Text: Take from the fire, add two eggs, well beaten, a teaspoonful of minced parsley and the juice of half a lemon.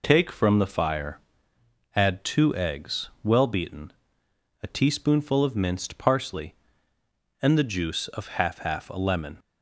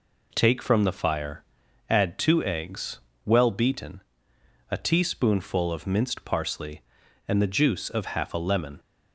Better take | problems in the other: second | says "half" twice; at 8.5 s

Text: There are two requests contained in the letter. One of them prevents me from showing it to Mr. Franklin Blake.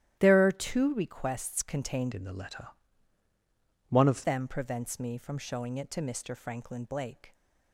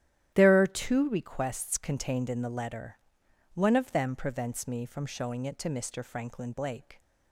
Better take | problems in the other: second | starts louder than the rest; strong; until 1.2 s; 13 dB; strong in the second // changes voice from "in" to "of"; from 2.1 to 4.2 s; 2.1 s long

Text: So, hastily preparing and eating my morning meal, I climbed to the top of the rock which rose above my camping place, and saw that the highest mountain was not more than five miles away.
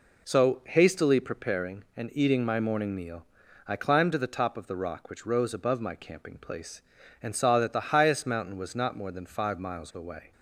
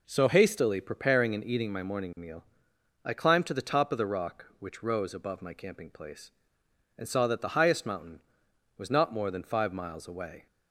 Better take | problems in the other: neither | none

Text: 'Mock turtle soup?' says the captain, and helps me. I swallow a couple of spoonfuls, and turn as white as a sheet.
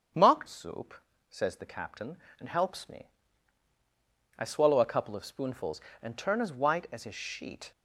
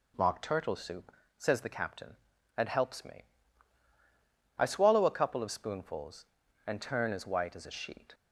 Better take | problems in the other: second | starts louder than the rest; strong; until 1.5 s; 8 dB // skips "turtle"; at 0.4 s

